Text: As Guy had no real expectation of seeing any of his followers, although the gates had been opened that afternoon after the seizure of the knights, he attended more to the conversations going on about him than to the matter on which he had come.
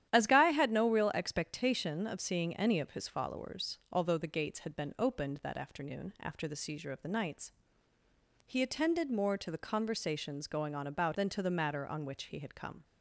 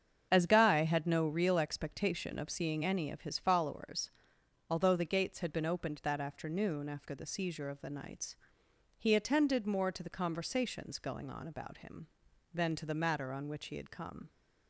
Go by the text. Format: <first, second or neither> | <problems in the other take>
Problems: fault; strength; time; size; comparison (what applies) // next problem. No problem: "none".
second | starts louder than the rest; strong; until 1.1 s; 11 dB; strong in the second // skips "him"; at 11.1 s